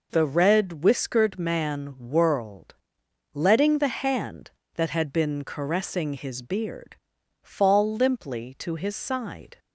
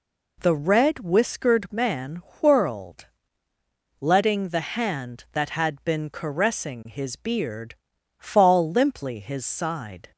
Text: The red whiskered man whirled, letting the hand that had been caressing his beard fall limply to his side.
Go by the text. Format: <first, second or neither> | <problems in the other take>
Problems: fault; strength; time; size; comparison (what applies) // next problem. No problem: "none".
first | pauses between "man" and "whirled"; slight; at 2.2 s; 0.18 s long // pauses between "beard" and "fall"; at 7.7 s; 0.44 s long; noticeable in the first // skips "to"; at 9.1 s